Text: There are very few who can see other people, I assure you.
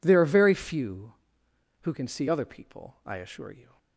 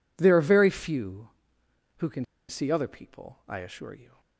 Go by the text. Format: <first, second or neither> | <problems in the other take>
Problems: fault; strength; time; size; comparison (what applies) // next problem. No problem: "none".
first | pauses between "can" and "see"; slight; at 2.2 s; 0.24 s long